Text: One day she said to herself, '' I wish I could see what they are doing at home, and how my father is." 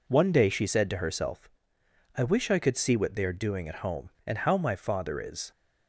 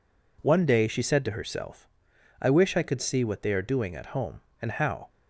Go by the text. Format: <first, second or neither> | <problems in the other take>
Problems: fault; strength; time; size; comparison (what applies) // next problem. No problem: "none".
first | stops before "my father is"; at 5.0 s